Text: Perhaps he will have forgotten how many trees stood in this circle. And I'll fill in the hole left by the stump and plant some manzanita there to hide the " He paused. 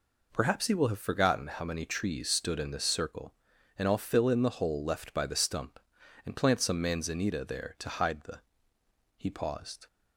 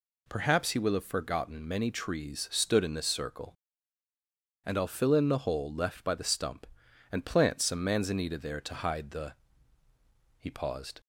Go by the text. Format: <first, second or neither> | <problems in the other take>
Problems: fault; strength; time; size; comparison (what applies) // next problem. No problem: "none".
first | skips "how"; at 1.6 s